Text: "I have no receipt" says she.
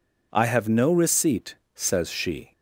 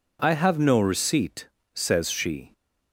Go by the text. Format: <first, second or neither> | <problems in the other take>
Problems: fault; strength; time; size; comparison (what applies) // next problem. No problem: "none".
neither | pauses between "receipt" and "says"; slight; the same in both